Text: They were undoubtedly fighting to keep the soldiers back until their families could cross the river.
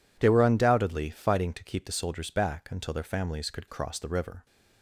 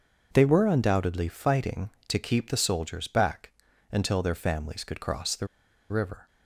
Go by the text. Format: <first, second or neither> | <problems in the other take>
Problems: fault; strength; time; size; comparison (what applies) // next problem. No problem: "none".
first | pauses between "back" and "until"; at 3.4 s; 0.42 s long // pauses between "the" and "river"; at 5.4 s; 0.43 s long